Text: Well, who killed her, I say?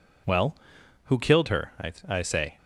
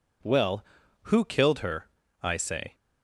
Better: second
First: says "I" twice; at 2.0 s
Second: none

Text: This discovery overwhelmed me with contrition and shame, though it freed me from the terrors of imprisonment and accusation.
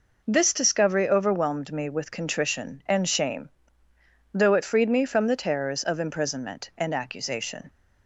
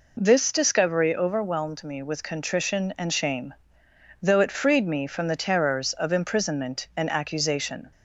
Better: neither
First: none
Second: none

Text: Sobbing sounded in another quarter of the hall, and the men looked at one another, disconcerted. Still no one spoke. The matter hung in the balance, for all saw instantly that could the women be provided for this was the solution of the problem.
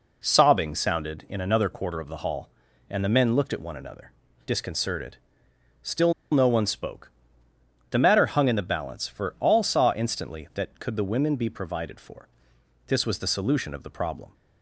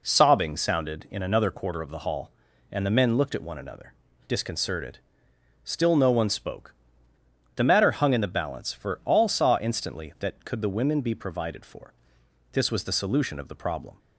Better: second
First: pauses between "Still" and "no"; slight; at 6.1 s; 0.19 s long // pauses between "for" and "this"; noticeable; at 12.2 s; 0.60 s long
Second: pauses between "for" and "this"; noticeable; at 11.9 s; 0.60 s long

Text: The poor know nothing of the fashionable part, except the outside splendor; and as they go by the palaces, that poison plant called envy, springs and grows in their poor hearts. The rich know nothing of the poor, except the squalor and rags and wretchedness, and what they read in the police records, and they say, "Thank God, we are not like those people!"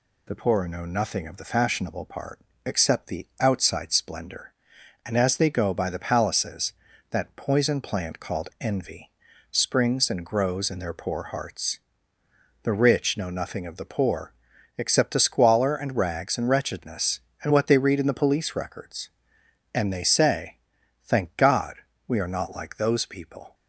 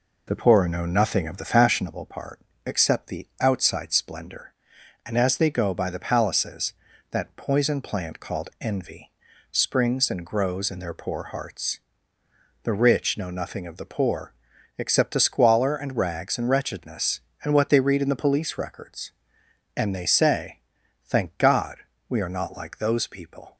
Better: first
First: none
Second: starts louder than the rest; noticeable; until 1.9 s; 4 dB

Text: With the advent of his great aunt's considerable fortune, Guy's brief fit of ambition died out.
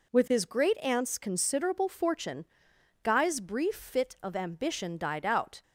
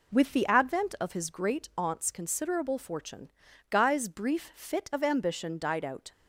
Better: second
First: skips "the advent of"; at 0.2 s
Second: none

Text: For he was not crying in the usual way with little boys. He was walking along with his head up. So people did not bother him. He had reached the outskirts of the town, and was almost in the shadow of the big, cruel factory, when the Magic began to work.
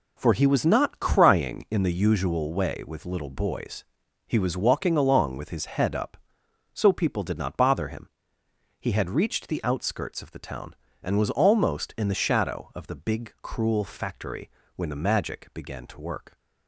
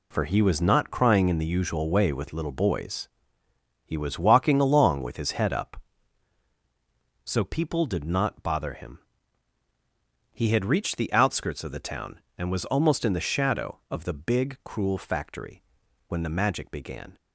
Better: first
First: none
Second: stops before "to work"; at 17.1 s

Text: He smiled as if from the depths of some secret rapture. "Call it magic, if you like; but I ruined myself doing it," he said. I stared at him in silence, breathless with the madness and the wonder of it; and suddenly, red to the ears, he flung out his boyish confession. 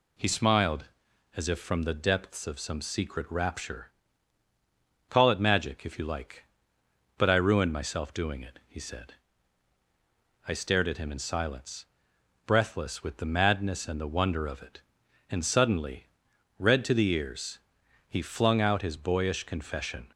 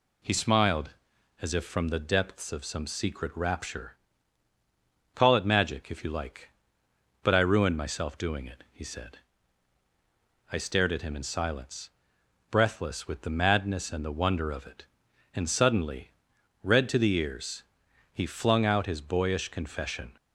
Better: neither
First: none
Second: none

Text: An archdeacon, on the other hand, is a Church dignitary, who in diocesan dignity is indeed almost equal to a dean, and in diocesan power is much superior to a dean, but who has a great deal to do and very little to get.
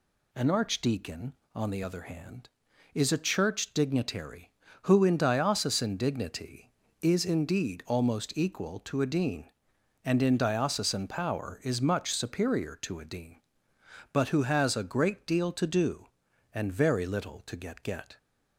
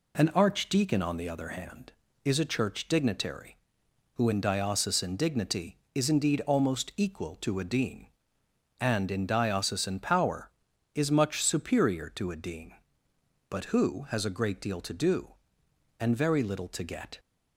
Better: second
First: says "get" twice; at 17.8 s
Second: none

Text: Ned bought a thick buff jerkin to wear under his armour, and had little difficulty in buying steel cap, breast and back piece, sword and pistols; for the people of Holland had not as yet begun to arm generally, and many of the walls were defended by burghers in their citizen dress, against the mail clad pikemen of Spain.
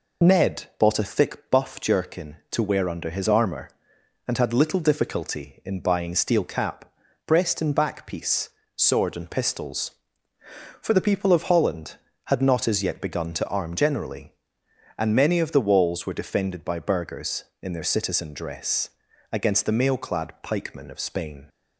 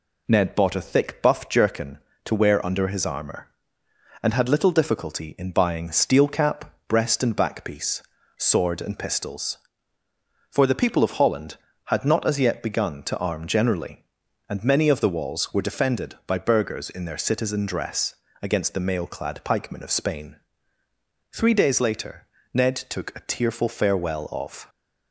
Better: first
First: none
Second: goes on to say "Three days later Ned took a tearful farewell of"; strong; from 21.3 s on; 3.3 s long

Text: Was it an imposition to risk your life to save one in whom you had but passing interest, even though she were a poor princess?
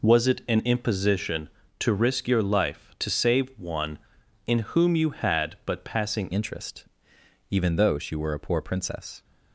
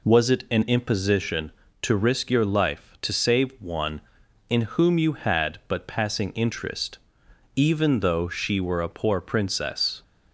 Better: second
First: changes voice at "interest"; from 6.3 s on; 2.9 s long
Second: none

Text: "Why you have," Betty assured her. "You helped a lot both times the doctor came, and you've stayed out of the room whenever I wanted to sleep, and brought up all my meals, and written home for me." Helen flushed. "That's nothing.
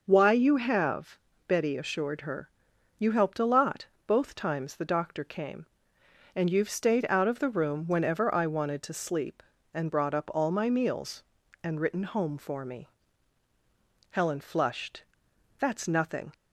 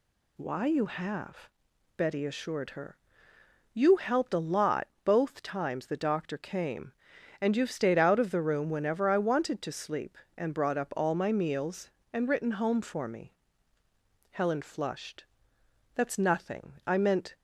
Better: first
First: pauses between "lot" and "both"; slight; at 3.8 s; 0.18 s long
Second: pauses between "lot" and "both"; slight; at 4.8 s; 0.20 s long // goes on to say "I meant"; from 16.8 s on; 0.50 s long

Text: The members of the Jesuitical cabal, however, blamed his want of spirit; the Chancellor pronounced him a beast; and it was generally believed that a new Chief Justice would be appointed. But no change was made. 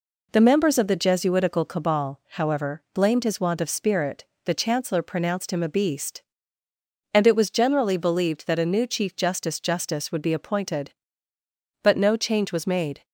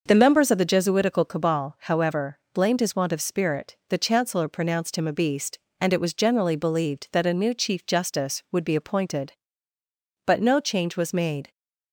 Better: second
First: says "Justice" twice; at 9.5 s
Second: none

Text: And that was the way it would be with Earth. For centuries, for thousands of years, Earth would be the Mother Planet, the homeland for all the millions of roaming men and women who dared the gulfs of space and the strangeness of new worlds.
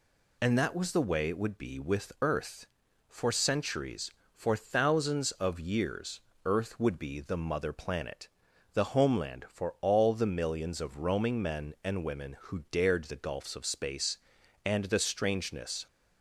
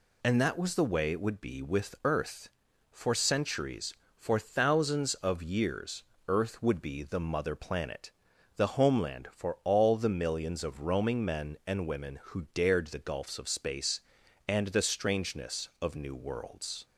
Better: second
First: stops before "of new worlds"; at 15.8 s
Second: none

